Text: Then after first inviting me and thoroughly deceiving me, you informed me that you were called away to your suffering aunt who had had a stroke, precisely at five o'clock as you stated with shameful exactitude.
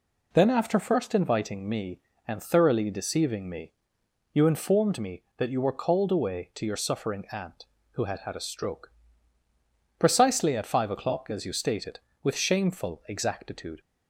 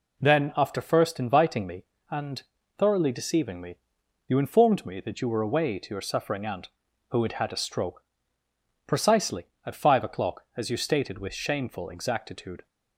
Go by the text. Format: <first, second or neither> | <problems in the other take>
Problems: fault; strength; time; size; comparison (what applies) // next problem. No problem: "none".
first | pauses between "and" and "thoroughly"; slight; at 2.4 s; 0.36 s long // skips "called"; at 5.4 s